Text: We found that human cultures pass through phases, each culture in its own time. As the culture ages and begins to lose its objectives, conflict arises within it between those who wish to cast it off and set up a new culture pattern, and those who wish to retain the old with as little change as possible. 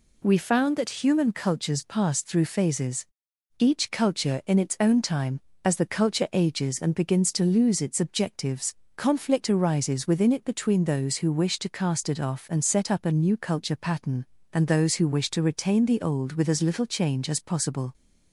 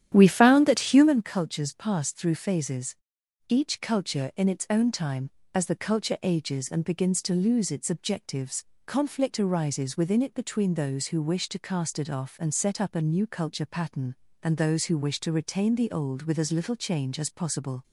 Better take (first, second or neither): first